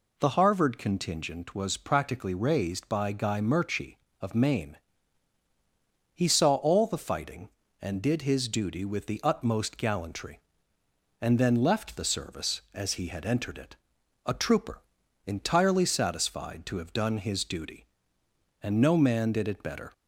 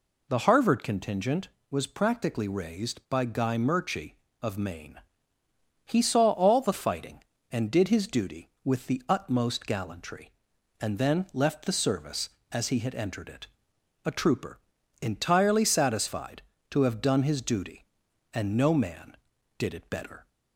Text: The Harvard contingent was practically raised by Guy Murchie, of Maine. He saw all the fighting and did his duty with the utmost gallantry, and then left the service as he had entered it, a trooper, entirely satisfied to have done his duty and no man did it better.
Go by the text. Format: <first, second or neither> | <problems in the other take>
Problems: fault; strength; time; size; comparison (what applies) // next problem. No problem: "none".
neither | none